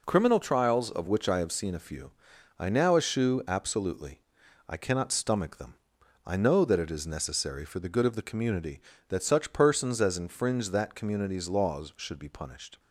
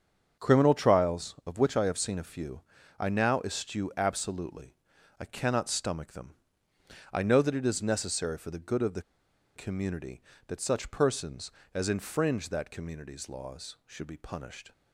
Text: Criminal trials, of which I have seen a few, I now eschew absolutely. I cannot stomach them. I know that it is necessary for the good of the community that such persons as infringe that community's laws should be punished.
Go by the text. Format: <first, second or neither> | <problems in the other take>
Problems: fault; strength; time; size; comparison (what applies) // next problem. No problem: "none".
first | starts louder than the rest; strong; until 1.5 s; 7 dB // pauses between "the" and "community"; noticeable; at 9.0 s; 0.53 s long